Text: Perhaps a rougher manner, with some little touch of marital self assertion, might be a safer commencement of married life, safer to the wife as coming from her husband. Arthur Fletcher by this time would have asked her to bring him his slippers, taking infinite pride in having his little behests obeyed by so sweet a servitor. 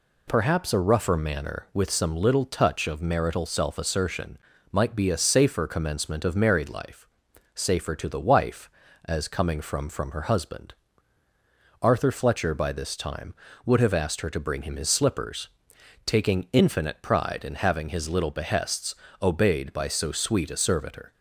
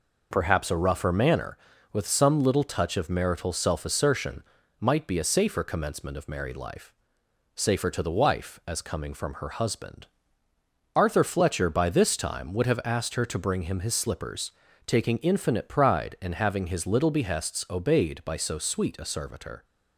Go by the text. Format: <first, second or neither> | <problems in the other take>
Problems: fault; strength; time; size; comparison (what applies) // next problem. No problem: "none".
second | says "from" twice; at 9.8 s // pauses between "behests" and "obeyed"; slight; at 18.9 s; 0.28 s long